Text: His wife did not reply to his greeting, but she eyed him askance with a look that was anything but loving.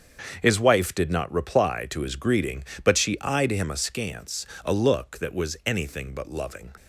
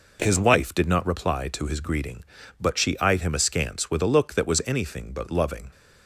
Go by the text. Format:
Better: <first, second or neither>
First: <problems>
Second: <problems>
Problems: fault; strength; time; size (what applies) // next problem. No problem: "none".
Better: second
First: starts louder than the rest; until 1.4 s; 7 dB // skips "with"; at 4.5 s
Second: none